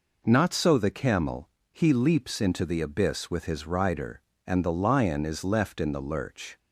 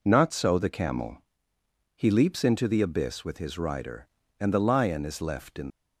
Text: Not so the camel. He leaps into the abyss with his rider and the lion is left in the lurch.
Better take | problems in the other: first | stops before "the lurch"; at 5.6 s

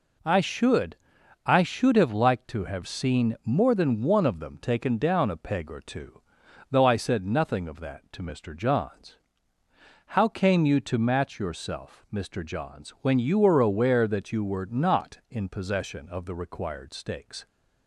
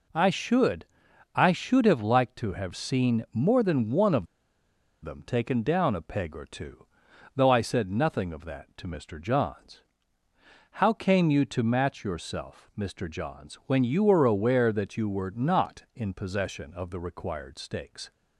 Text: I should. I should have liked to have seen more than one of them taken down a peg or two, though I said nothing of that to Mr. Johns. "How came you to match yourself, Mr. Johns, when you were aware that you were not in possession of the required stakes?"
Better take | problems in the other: first | pauses between "of" and "them"; noticeable; at 4.2 s; 0.77 s long

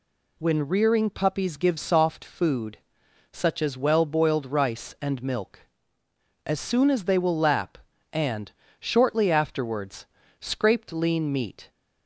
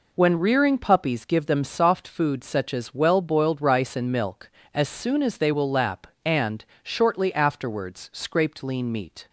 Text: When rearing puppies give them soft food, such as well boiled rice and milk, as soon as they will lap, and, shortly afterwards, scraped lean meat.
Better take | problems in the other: second | skips "them"; at 1.7 s

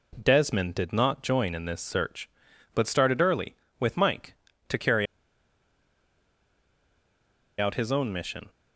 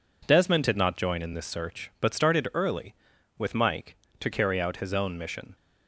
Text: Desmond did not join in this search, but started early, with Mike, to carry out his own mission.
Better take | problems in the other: second | pauses between "carry" and "out"; strong; at 5.0 s; 2.5 s long

